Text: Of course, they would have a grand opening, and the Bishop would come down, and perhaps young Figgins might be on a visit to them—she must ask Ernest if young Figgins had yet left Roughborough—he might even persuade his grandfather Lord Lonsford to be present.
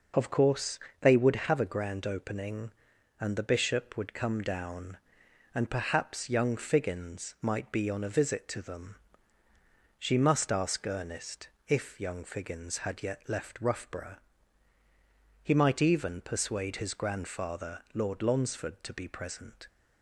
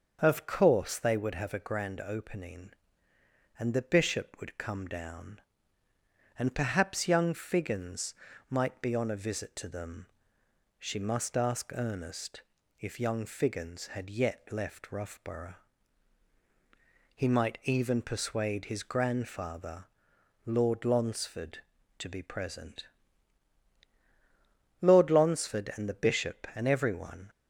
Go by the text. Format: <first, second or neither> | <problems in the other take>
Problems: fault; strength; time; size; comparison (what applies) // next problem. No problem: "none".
first | starts louder than the rest; until 1.2 s; 6.5 dB // pauses between "Figgins" and "might"; slight; at 8.1 s; 0.36 s long // pauses between "Ernest" and "if"; at 12.4 s; 0.38 s long; slight in the first // pauses between "grandfather" and "Lord"; noticeable; at 19.8 s; 0.60 s long // goes on to say "Lord Lonsford and the Bishop and everyone"; strong; from 24.7 s on; 2.5 s long